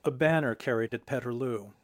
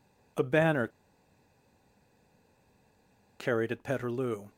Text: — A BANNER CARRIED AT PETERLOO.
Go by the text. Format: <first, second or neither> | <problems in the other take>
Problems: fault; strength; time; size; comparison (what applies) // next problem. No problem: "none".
first | pauses between "BANNER" and "CARRIED"; strong; at 0.8 s; 2.5 s long